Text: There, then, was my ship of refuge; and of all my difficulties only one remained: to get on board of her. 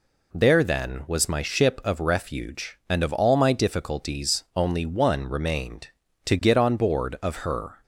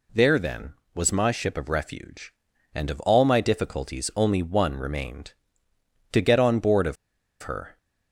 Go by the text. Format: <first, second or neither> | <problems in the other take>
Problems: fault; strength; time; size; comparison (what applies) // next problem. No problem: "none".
first | pauses between "of" and "her"; noticeable; at 6.9 s; 0.47 s long